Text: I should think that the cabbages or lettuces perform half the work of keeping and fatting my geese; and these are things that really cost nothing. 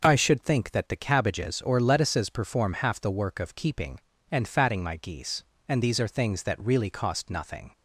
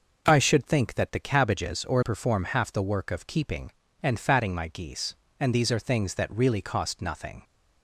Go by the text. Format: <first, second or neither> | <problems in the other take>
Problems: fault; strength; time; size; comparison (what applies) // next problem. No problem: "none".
first | skips "lettuces"; at 2.0 s